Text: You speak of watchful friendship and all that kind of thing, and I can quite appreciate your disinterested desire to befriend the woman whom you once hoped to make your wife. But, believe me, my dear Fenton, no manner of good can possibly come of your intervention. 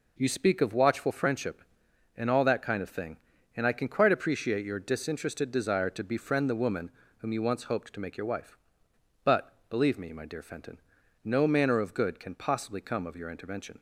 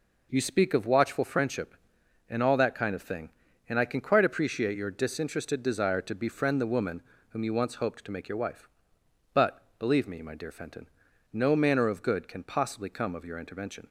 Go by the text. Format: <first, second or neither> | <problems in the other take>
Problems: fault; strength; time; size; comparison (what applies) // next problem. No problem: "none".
neither | pauses between "woman" and "whom"; slight; the same in both